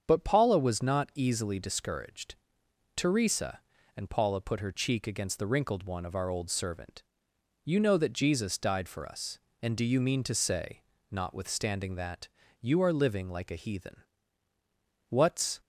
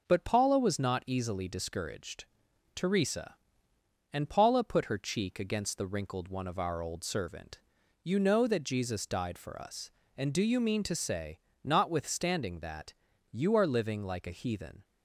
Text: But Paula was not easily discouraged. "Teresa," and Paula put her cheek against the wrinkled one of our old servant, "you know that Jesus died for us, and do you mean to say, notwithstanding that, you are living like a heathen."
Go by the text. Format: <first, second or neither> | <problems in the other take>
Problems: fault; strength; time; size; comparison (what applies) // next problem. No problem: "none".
second | starts louder than the rest; strong; until 1.0 s; 7.5 dB // goes on to say "What's"; from 15.0 s on; 0.52 s long